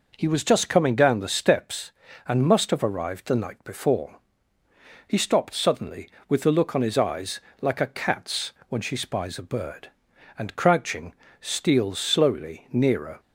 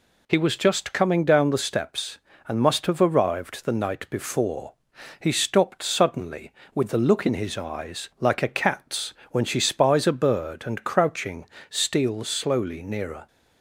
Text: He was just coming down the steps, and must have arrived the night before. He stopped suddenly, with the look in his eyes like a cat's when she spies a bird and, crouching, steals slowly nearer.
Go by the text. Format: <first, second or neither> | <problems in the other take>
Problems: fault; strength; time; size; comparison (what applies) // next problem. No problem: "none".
second | says "on" for "in"; at 6.7 s // pauses between "eyes" and "like"; slight; at 7.3 s; 0.20 s long // pauses between "cat's" and "when"; slight; at 8.5 s; 0.16 s long; slight in the second